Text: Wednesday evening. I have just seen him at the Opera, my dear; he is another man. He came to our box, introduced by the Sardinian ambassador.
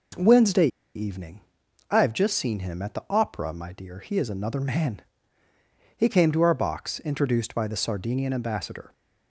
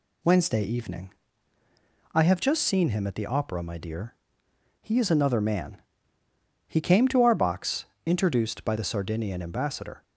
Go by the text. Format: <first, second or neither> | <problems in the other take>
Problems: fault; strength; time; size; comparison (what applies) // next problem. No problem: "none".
second | pauses between "Wednesday" and "evening"; slight; at 0.6 s; 0.28 s long